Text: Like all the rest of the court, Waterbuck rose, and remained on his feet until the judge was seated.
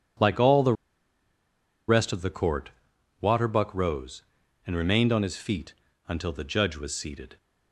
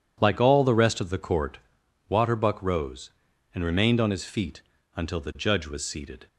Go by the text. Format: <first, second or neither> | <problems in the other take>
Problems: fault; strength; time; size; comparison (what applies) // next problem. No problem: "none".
second | pauses between "the" and "rest"; at 0.7 s; 1.1 s long // pauses between "feet" and "until"; slight; at 5.7 s; 0.36 s long; slight in the second